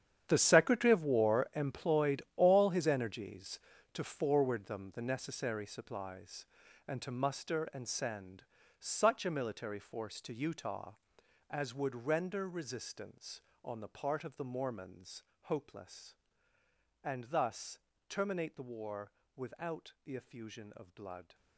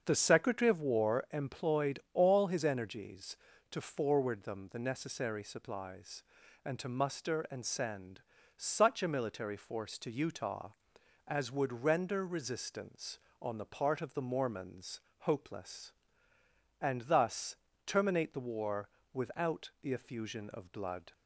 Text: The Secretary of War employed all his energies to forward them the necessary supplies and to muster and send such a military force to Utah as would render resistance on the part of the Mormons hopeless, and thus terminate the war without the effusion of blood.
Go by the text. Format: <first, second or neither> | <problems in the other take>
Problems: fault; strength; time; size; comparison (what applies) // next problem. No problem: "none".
second | gets quieter; strong; throughout; 15 dB // starts louder than the rest; strong; until 1.2 s; 9 dB; also in the second // pauses between "send" and "such"; at 8.4 s; 0.38 s long; also in the second // pauses between "Mormons" and "hopeless"; slight; at 15.2 s; 0.20 s long; slight in the second // pauses between "thus" and "terminate"; slight; at 17.7 s; 0.30 s long; slight in the second // pauses between "war" and "without"; slight; at 19.1 s; 0.24 s long; slight in the second